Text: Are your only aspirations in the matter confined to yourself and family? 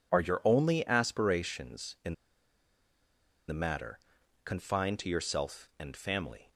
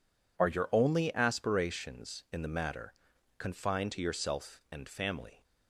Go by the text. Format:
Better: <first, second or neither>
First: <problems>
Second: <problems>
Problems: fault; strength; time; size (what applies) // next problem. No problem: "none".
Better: second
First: pauses between "in" and "the"; strong; at 2.1 s; 1.3 s long // pauses between "matter" and "confined"; noticeable; at 3.9 s; 0.46 s long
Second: pauses between "matter" and "confined"; at 2.9 s; 0.45 s long